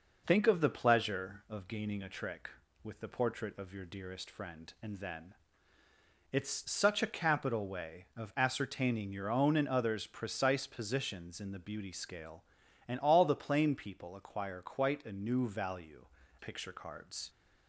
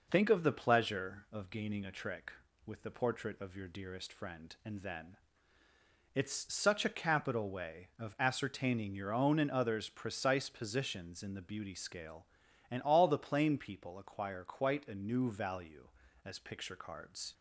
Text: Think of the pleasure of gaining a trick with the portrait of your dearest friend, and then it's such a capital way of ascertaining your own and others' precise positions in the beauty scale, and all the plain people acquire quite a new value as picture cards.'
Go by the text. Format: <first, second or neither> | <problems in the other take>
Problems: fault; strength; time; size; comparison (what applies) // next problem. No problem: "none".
second | pauses between "then" and "it's"; noticeable; at 5.3 s; 0.98 s long; noticeable in the second // skips "as"; at 16.2 s